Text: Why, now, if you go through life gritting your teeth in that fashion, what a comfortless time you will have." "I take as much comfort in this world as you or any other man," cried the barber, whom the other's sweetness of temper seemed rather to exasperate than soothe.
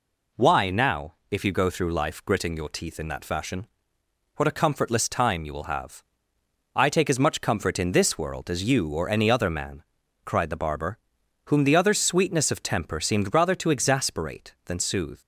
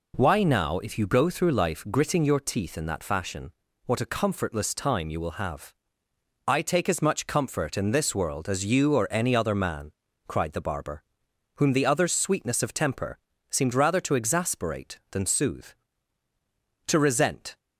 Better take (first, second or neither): first